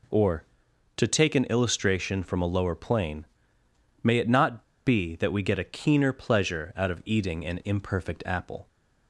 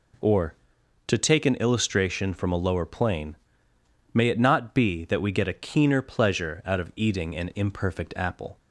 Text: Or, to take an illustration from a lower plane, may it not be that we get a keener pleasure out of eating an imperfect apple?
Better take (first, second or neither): second